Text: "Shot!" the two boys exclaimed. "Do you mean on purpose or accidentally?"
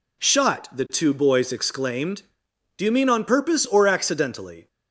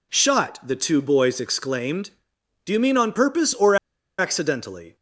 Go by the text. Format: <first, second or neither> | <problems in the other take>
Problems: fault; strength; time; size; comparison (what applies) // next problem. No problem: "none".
first | pauses between "or" and "accidentally"; at 3.7 s; 0.43 s long